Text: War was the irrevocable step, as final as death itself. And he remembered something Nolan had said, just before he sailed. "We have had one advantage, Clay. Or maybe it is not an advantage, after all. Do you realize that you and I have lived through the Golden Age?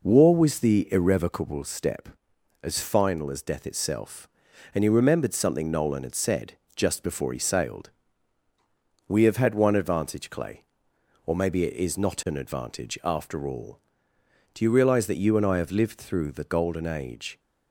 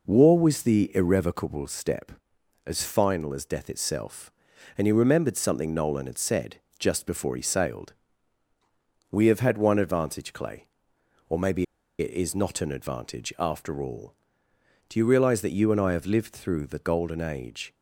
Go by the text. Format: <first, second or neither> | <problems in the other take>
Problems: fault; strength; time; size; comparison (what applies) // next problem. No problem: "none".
first | pauses between "maybe" and "it"; slight; at 11.6 s; 0.35 s long